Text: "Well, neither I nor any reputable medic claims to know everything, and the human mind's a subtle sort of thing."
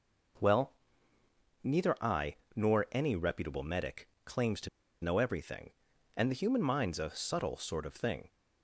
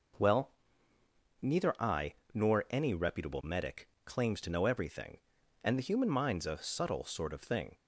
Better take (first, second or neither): second